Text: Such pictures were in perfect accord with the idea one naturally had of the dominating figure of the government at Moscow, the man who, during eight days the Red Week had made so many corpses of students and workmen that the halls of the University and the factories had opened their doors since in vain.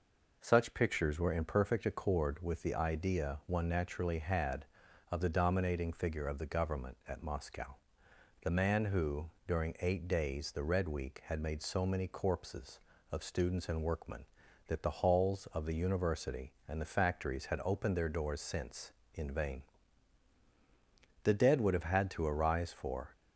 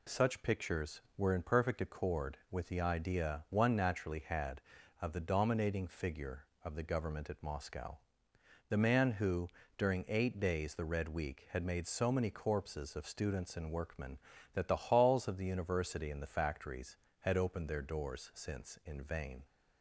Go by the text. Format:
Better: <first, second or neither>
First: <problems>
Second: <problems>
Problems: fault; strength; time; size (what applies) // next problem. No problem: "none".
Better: second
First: goes on to say "The dead would have had to arise for"; strong; from 21.2 s on; 1.8 s long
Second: none